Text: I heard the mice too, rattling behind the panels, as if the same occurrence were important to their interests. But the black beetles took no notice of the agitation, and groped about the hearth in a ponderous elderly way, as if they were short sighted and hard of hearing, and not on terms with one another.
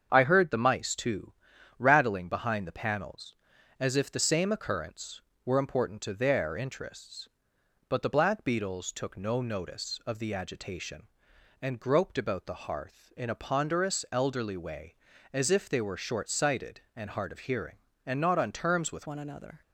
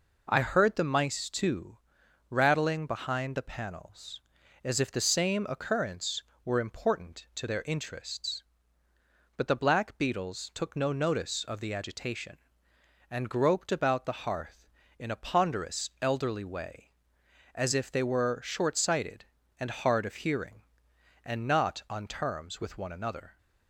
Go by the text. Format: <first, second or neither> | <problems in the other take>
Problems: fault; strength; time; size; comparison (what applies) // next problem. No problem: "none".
second | starts louder than the rest; strong; until 1.1 s; 7.5 dB // changes voice at "one"; from 19.0 s on; 0.6 s long